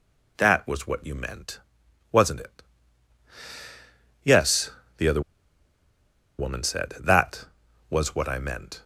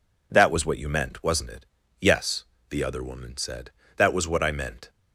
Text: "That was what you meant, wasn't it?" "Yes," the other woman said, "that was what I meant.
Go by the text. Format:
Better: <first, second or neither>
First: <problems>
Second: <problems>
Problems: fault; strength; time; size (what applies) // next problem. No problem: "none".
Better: second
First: pauses between "other" and "woman"; at 5.2 s; 1.1 s long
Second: none